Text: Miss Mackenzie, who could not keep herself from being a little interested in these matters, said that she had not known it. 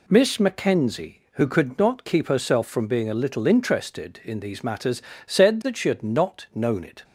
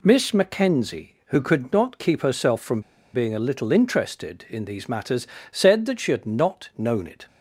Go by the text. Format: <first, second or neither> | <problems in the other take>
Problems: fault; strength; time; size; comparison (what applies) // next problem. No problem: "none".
first | pauses between "from" and "being"; slight; at 2.8 s; 0.33 s long